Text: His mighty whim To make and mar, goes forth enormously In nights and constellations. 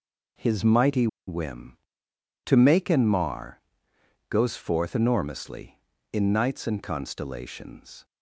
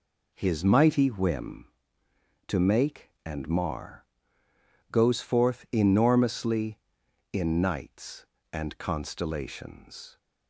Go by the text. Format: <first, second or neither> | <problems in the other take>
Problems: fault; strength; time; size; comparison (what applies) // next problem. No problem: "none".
second | pauses between "mighty" and "whim"; slight; at 1.0 s; 0.20 s long